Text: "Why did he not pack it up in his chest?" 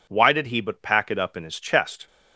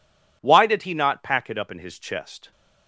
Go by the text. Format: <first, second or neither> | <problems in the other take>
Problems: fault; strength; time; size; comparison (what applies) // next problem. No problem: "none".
second | says "but" for "not"; at 0.6 s